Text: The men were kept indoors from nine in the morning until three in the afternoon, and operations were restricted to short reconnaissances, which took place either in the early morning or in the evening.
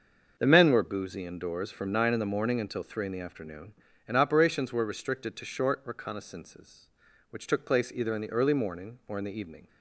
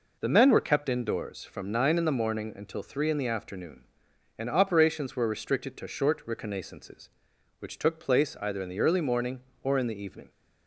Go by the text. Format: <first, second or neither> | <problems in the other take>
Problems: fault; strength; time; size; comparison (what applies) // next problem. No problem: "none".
second | starts louder than the rest; until 1.3 s; 6.5 dB // says "boozy" for "kept"; at 0.8 s